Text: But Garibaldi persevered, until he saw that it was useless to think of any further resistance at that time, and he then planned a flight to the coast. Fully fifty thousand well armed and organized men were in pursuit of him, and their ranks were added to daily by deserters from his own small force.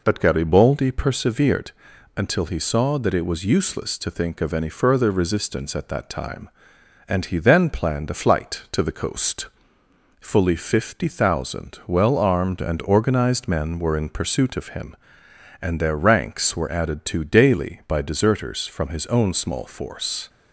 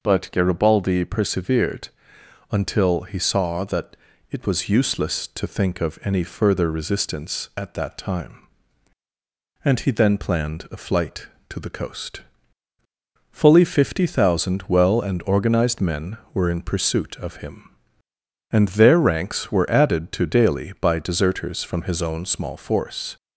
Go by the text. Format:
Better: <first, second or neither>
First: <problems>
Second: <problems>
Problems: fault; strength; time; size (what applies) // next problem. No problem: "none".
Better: first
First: none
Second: pauses between "that" and "it"; slight; at 3.9 s; 0.34 s long // skips "armed"; at 14.9 s